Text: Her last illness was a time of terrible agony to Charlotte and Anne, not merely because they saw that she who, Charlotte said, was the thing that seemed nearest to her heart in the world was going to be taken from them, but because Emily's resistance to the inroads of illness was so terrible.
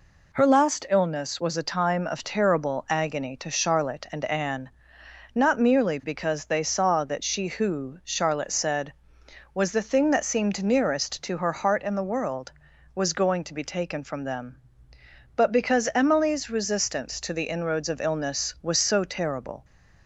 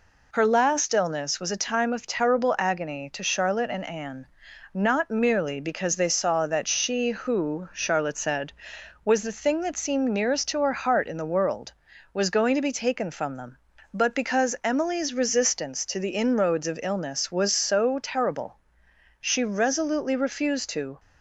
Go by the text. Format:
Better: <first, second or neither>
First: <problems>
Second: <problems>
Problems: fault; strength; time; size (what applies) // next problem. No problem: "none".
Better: first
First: none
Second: goes on to say "She resolutely refused to"; strong; from 19.1 s on; 1.8 s long